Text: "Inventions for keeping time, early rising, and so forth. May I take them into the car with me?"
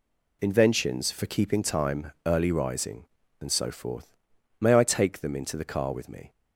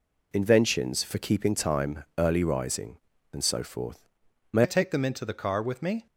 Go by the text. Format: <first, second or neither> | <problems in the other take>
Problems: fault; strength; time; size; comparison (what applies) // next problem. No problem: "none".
first | changes voice at "I"; from 4.6 s on; 1.4 s long